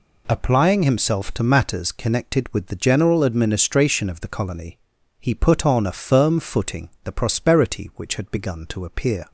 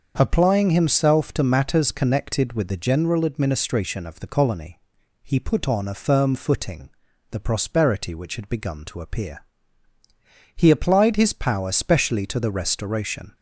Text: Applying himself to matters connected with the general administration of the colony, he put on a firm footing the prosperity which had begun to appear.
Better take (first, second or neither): first